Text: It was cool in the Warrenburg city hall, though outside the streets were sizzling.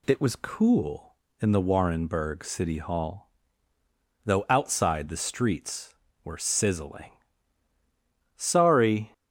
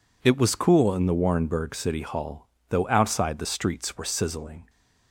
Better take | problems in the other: second | goes on to say "Sorry"; noticeable; from 8.3 s on; 0.76 s long

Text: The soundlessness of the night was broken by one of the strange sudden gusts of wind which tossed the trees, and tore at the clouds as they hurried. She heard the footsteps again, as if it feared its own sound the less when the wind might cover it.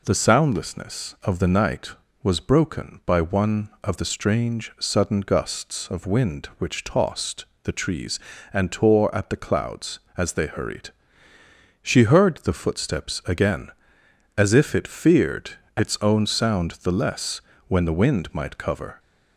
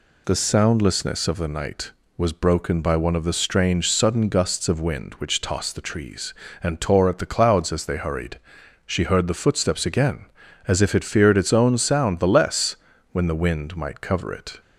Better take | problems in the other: second | pauses between "tossed" and "the"; slight; at 7.4 s; 0.18 s long // pauses between "feared" and "its"; slight; at 15.5 s; 0.26 s long // pauses between "less" and "when"; slight; at 17.3 s; 0.30 s long; slight in the second // stops before "it"; at 18.9 s

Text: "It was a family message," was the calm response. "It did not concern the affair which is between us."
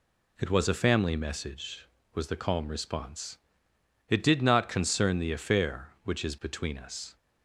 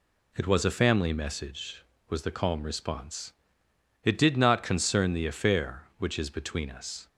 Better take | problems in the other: neither | none

